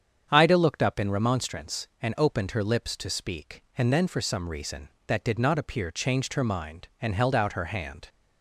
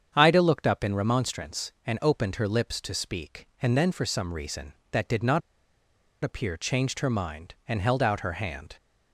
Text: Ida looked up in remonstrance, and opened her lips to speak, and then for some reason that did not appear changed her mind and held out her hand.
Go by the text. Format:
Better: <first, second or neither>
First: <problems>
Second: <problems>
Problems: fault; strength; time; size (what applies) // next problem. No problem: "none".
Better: first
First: starts louder than the rest; strong; until 1.3 s; 8 dB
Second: starts louder than the rest; strong; until 1.1 s; 7.5 dB // pauses between "not" and "appear"; noticeable; at 5.4 s; 0.81 s long